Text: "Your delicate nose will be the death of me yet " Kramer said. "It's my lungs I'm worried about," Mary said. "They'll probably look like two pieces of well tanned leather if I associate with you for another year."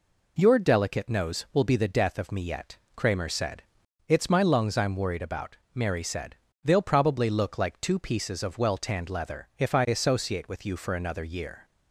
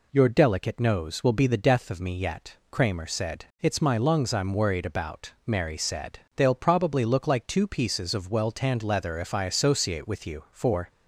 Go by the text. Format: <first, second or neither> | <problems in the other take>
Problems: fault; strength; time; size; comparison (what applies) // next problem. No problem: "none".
first | stops before "another year"; at 10.8 s